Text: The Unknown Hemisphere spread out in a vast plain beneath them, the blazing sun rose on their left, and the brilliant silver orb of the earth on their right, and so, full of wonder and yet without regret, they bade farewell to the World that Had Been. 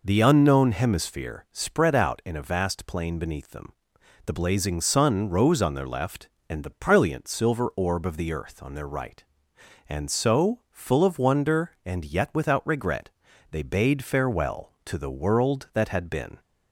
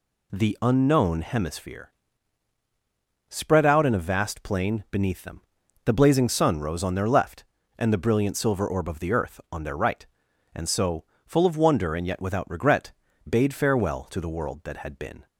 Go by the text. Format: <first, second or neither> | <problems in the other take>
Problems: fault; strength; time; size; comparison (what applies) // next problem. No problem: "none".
first | pauses between "Hemisphere" and "spread"; strong; at 1.8 s; 1.4 s long // skips "they"; at 13.0 s